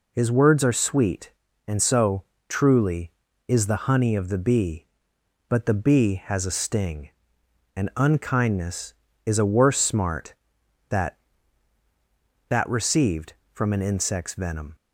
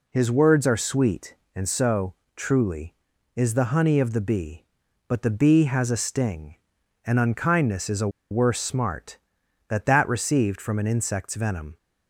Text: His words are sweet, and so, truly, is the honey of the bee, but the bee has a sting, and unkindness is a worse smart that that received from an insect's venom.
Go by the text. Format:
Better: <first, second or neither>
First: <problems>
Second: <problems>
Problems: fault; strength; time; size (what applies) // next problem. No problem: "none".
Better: first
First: none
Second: pauses between "a" and "worse"; slight; at 8.0 s; 0.21 s long